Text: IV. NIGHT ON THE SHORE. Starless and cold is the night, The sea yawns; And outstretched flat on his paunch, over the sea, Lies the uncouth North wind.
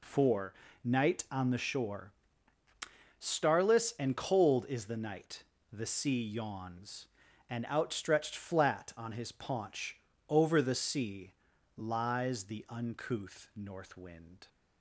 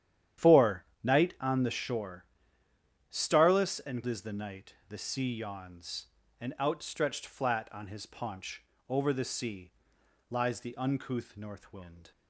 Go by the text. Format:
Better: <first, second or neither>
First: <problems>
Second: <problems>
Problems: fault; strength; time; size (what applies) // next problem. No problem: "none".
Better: first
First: none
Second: starts louder than the rest; strong; until 1.6 s; 10 dB // skips "cold"; at 4.0 s